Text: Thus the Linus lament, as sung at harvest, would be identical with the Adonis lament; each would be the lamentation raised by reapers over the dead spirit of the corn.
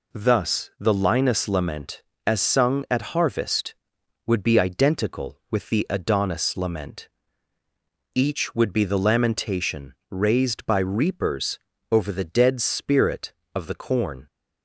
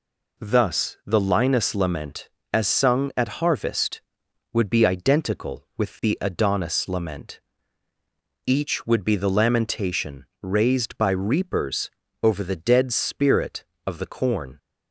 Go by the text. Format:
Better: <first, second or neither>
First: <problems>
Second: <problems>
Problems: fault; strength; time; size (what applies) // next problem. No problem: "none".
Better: neither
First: pauses between "lamentation" and "raised"; slight; at 9.9 s; 0.16 s long // pauses between "reapers" and "over"; slight; at 11.6 s; 0.32 s long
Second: pauses between "lamentation" and "raised"; slight; at 10.2 s; 0.16 s long // pauses between "reapers" and "over"; slight; at 11.9 s; 0.32 s long